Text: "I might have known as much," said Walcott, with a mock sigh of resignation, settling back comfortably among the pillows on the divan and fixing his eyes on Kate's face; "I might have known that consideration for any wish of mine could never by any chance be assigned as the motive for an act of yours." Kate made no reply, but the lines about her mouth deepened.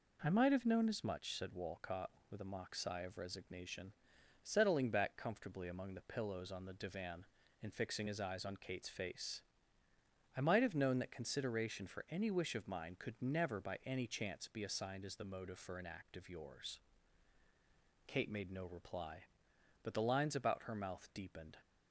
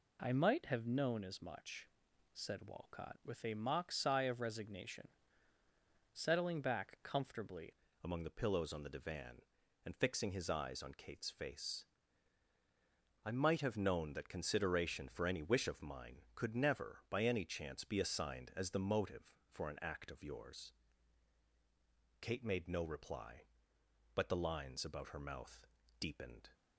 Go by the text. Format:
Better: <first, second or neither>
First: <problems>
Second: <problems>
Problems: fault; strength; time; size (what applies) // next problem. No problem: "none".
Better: first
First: none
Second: changes voice at "among"; from 8.0 s on; 18.4 s long // pauses between "mouth" and "deepened"; slight; at 25.6 s; 0.32 s long